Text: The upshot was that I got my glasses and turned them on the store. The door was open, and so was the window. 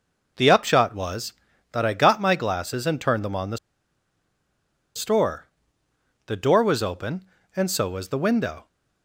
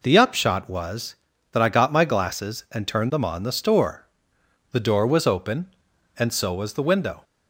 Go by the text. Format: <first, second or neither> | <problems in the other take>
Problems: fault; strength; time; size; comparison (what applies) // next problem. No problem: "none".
second | pauses between "the" and "store"; strong; at 3.5 s; 1.3 s long